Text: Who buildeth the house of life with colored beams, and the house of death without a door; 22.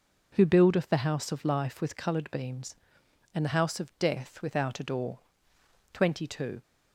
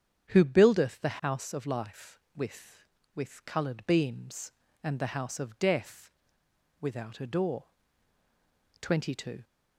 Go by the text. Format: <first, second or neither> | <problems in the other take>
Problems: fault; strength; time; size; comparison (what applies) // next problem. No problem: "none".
first | starts louder than the rest; strong; until 1.3 s; 8 dB // says "with" twice; at 3.1 s // pauses between "death" and "without"; noticeable; at 6.1 s; 0.68 s long